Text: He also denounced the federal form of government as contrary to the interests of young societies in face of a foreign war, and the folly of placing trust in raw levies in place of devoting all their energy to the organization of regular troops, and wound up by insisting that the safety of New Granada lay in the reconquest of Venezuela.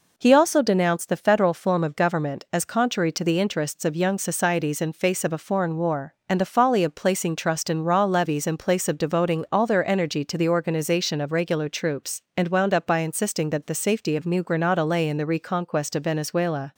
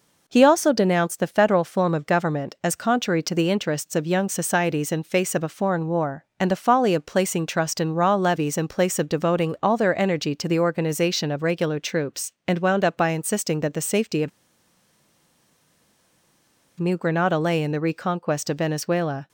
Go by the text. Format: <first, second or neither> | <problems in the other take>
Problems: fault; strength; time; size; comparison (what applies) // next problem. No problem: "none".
first | pauses between "of" and "New"; strong; at 14.2 s; 2.5 s long